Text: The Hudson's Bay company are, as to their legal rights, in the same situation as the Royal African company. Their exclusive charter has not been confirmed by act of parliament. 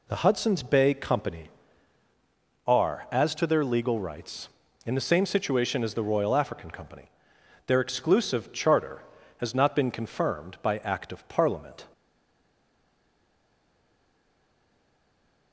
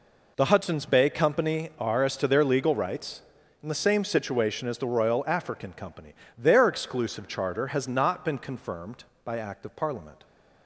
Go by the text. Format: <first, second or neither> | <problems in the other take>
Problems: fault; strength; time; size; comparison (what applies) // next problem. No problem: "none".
second | stays silent after the last word; strong; from 11.9 s on; 3.6 s long